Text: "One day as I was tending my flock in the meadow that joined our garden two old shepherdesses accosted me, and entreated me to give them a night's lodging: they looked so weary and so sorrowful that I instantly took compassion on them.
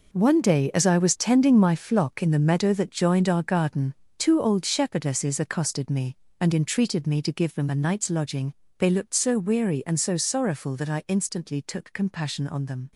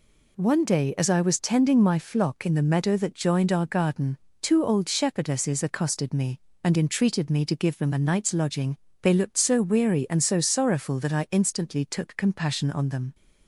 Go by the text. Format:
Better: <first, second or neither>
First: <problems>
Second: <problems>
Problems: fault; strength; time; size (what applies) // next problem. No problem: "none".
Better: second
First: gets quieter; strong; throughout; 11 dB // pauses between "garden" and "two"; slight; at 3.9 s; 0.22 s long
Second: pauses between "garden" and "two"; slight; at 4.1 s; 0.22 s long